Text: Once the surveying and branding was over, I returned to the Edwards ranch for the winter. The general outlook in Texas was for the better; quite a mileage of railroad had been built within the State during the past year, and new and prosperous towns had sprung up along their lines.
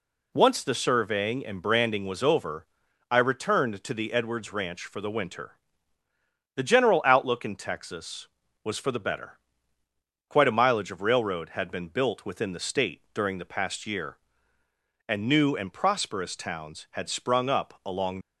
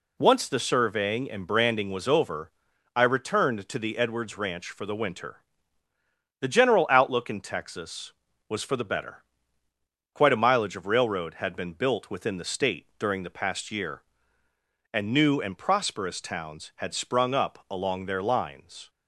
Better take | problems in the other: second | stops before "their lines"; at 18.2 s

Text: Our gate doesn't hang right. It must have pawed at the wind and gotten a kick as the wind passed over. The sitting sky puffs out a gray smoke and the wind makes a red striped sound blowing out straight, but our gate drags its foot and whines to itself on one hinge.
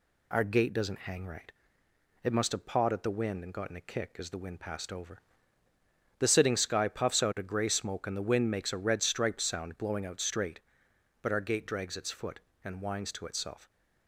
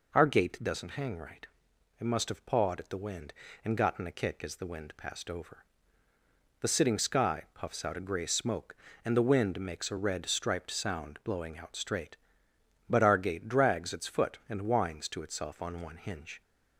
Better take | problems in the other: second | stops before "on one hinge"; at 13.6 s

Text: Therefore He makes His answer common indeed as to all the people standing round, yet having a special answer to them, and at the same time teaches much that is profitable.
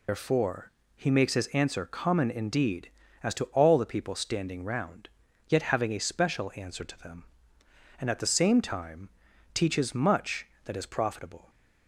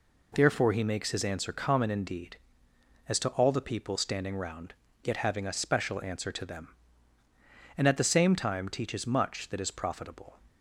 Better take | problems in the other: second | loses the start of "Therefore"; at 0.0 s; 135 ms // pauses between "Therefore" and "He"; slight; at 0.7 s; 0.24 s long // pauses between "time" and "teaches"; at 9.0 s; 0.44 s long

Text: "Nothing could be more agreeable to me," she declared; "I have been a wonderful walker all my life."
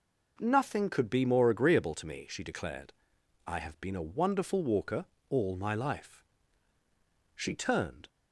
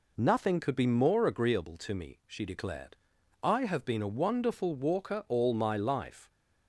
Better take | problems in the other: second | pauses between "walker" and "all"; slight; at 5.0 s; 0.24 s long // goes on to say "She turned"; noticeable; from 7.3 s on; 0.74 s long

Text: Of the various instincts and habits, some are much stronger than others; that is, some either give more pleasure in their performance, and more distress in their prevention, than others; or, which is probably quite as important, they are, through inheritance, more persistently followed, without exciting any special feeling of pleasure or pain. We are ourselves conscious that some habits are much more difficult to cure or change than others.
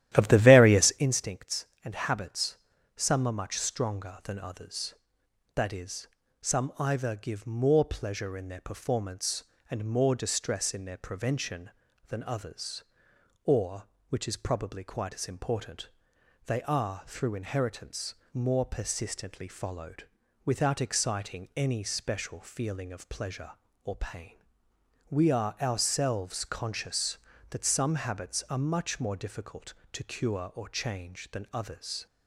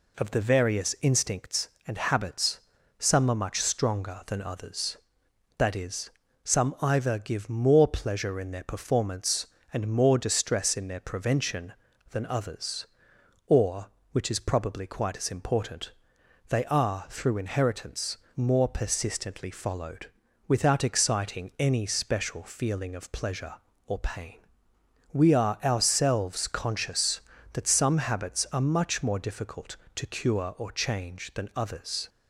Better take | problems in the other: second | starts louder than the rest; strong; until 1.0 s; 12.5 dB

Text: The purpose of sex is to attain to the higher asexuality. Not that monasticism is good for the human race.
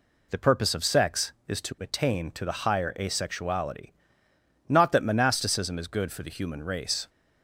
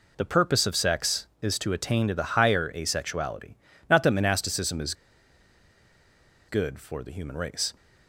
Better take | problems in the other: first | pauses between "is" and "good"; strong; at 4.9 s; 1.5 s long

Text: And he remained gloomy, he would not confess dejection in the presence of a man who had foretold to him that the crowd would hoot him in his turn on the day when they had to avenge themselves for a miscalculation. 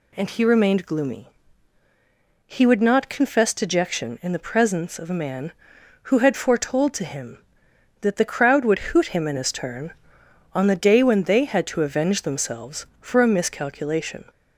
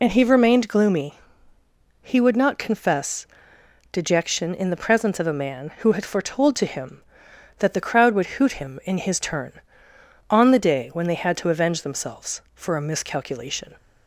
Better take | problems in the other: first | loses the start of "And"; at 0.0 s; 40 ms // pauses between "confess" and "dejection"; noticeable; at 3.2 s; 0.64 s long

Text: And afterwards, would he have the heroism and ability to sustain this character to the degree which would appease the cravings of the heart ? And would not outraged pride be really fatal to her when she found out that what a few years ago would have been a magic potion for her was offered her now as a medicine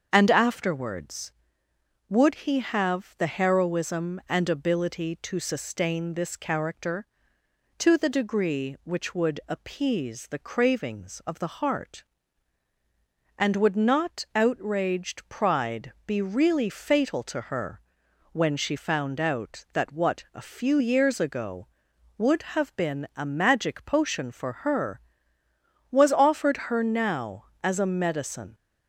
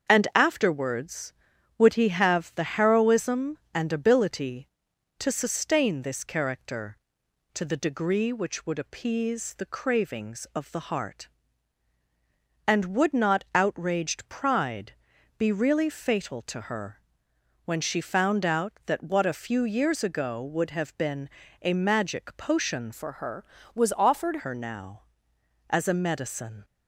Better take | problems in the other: first | starts louder than the rest; strong; until 1.1 s; 7 dB; also in the first // pauses between "pride" and "be"; noticeable; at 14.9 s; 0.46 s long // pauses between "her" and "when"; noticeable; at 17.0 s; 0.64 s long; noticeable in the first // pauses between "been" and "a"; slight; at 21.2 s; 0.34 s long // changes voice from "for" to "offered"; from 22.9 to 24.3 s; 1.4 s long

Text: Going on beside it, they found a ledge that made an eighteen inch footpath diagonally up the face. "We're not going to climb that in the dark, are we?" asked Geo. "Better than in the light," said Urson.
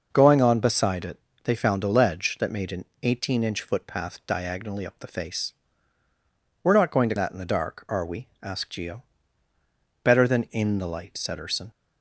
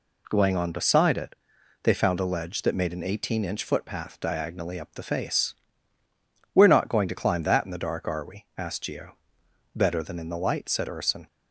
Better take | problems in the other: second | pauses between "an" and "eighteen"; slight; at 2.8 s; 0.20 s long // skips "climb"; at 7.1 s

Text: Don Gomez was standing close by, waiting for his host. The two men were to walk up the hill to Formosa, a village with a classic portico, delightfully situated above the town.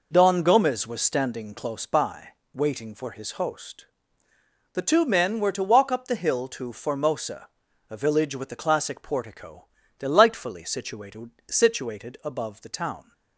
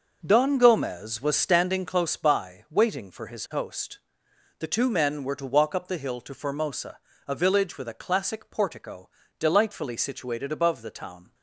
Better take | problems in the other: second | says "situated" twice; at 11.4 s

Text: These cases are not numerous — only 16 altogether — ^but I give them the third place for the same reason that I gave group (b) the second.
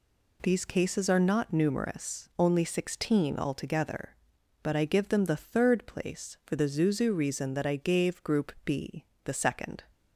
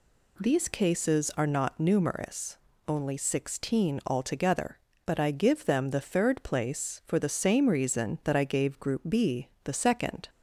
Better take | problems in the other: second | says "zuzu" for "same"; at 6.6 s

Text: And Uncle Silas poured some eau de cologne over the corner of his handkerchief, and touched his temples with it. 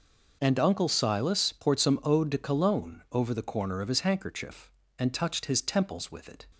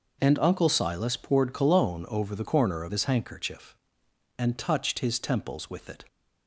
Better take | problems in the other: first | skips "some eau de"; at 1.5 s

